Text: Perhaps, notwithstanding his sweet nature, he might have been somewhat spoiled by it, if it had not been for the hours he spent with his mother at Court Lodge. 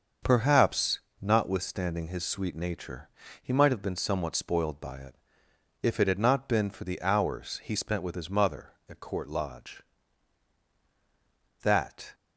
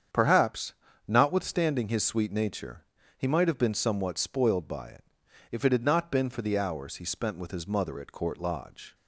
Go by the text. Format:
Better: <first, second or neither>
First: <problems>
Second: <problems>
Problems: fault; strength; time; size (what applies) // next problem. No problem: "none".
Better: second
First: starts louder than the rest; until 1.4 s; 6.5 dB // goes on to say "That"; from 11.6 s on; 0.52 s long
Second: starts louder than the rest; strong; until 1.4 s; 8 dB